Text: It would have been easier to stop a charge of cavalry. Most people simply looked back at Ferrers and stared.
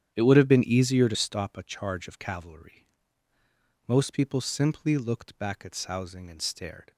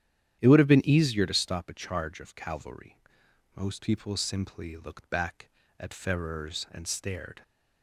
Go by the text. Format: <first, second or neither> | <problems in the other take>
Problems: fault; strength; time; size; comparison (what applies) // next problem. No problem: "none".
second | starts louder than the rest; strong; until 1.1 s; 9.5 dB; strong in the second // says "Sousing" for "Ferrers"; at 5.7 s